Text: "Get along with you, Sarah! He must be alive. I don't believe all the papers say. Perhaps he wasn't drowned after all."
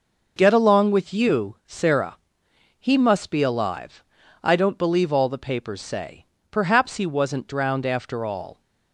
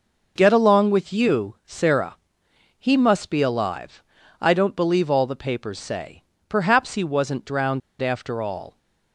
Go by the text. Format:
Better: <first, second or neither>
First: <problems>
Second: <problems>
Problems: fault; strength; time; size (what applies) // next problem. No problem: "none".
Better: first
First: none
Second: pauses between "drowned" and "after"; slight; at 7.8 s; 0.21 s long